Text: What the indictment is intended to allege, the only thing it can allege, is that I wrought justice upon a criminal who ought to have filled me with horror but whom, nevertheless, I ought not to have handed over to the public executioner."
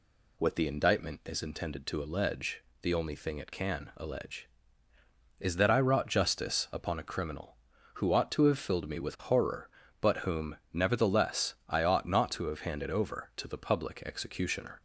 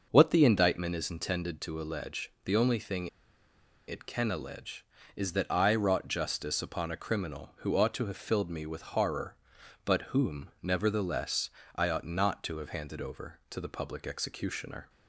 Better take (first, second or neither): first